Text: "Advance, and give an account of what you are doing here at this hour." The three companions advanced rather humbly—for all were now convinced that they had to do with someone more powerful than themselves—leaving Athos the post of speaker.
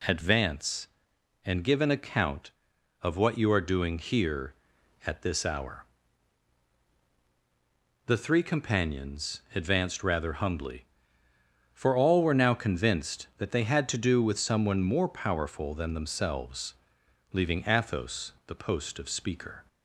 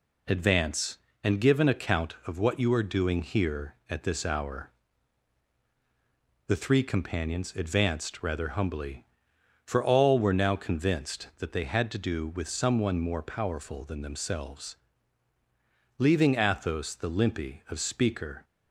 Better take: first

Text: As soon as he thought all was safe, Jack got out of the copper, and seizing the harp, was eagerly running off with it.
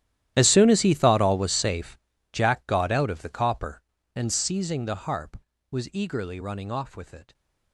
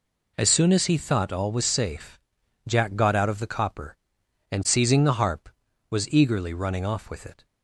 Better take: second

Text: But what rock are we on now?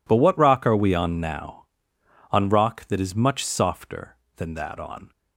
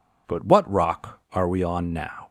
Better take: second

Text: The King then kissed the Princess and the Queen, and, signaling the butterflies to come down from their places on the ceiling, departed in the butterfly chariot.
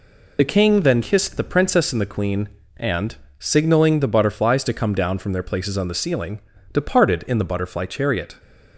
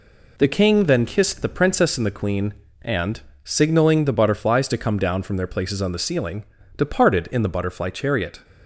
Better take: second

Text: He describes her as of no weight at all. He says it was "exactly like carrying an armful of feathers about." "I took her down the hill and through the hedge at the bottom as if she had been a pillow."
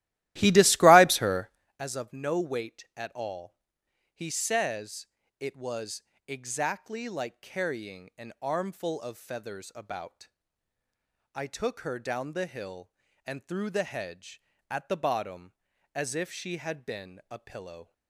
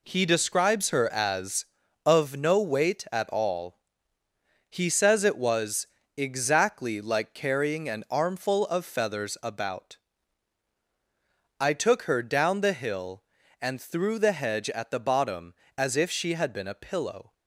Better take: second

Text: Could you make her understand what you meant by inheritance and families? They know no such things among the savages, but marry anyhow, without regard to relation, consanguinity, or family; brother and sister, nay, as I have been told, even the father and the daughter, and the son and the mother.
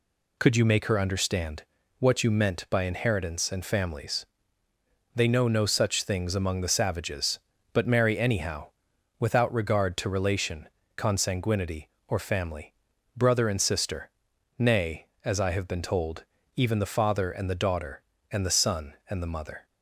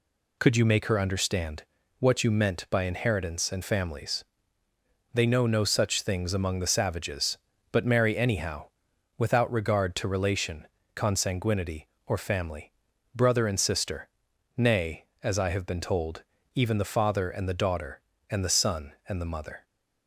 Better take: neither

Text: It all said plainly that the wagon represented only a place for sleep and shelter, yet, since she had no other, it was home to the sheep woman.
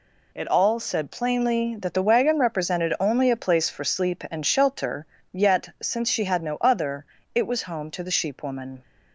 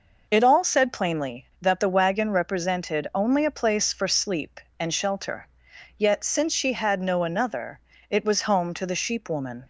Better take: first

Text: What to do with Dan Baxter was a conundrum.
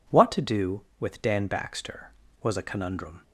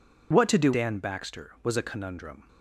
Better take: first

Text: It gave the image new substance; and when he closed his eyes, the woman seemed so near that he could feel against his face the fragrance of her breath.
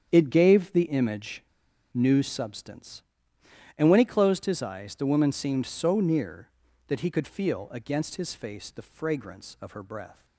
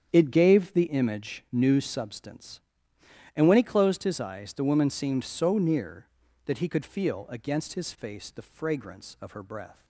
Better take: second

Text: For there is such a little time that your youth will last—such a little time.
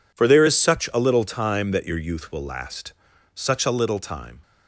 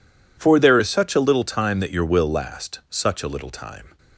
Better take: first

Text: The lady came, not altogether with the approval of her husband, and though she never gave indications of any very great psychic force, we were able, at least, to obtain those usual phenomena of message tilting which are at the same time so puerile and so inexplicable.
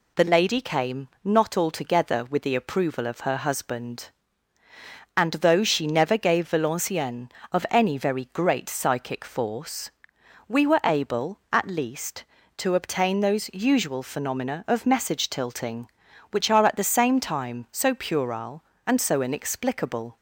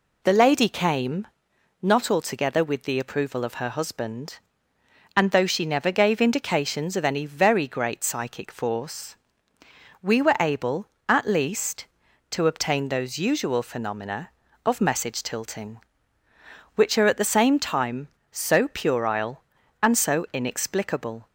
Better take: second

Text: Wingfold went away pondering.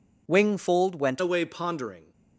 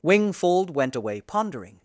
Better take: second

